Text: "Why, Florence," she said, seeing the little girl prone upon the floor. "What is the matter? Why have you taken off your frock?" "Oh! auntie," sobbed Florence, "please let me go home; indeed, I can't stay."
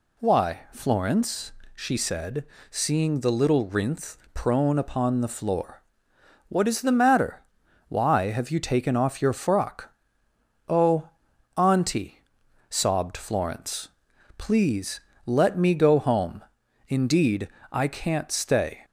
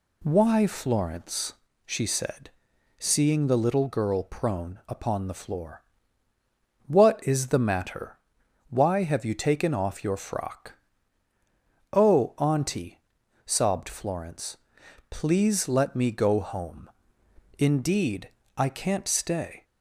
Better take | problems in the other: second | says "rinth" for "girl"; at 3.6 s // pauses between "please" and "let"; slight; at 15.0 s; 0.26 s long

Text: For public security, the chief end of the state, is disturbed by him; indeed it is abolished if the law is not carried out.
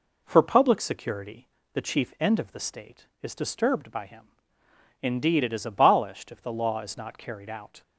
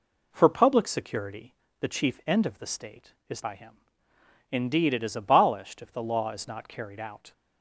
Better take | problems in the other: first | skips "disturbed"; at 3.4 s

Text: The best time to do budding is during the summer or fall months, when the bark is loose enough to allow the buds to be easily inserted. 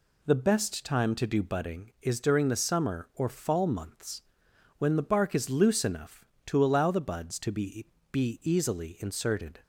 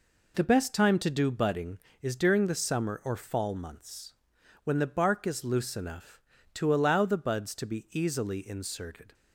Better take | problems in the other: second | says "be" twice; at 8.1 s

